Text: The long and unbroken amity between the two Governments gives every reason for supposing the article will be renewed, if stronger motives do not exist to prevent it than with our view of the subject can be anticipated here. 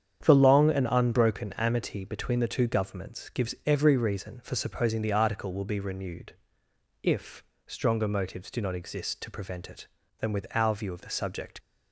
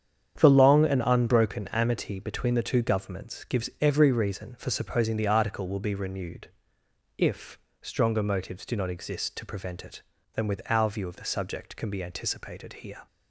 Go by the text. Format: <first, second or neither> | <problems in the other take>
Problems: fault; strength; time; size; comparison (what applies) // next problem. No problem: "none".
second | starts louder than the rest; strong; until 1.2 s; 8.5 dB; strong in the second // pauses between "if" and "stronger"; slight; at 7.4 s; 0.22 s long; slight in the second // stops before "can be anticipated here"; at 11.5 s